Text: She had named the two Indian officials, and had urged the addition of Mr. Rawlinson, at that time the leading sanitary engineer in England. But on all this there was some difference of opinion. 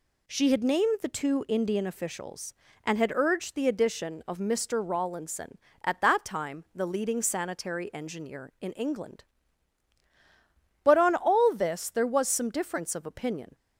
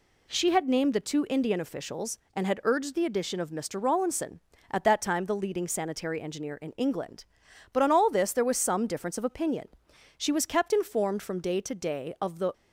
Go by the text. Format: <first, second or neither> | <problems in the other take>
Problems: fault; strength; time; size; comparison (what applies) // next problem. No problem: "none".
first | goes on to say "She was kept informed from day to day of the"; strong; from 10.1 s on; 2.3 s long